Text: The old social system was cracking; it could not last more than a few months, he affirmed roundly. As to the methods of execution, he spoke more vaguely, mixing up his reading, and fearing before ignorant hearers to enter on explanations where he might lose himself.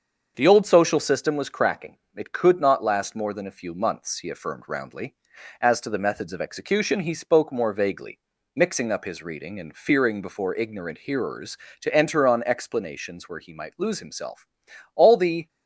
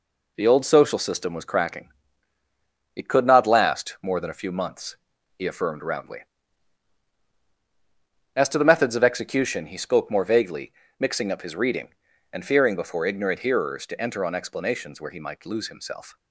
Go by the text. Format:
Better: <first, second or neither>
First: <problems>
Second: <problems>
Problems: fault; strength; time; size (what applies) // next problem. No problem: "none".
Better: second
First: starts louder than the rest; until 1.3 s; 6.5 dB // goes on to say "All the"; from 14.9 s on; 0.54 s long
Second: none